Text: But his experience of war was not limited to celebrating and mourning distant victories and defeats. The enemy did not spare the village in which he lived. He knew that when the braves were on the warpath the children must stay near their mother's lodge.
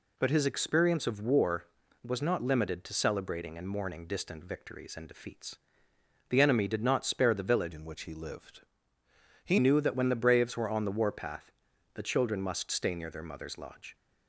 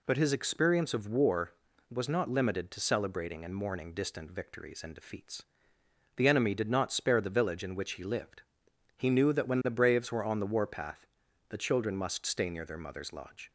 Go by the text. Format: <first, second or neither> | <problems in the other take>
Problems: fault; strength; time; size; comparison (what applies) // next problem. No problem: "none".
second | changes voice from "in" to "He"; from 7.7 to 9.5 s; 1.8 s long // pauses between "warpath" and "the"; at 11.5 s; 0.44 s long; also in the second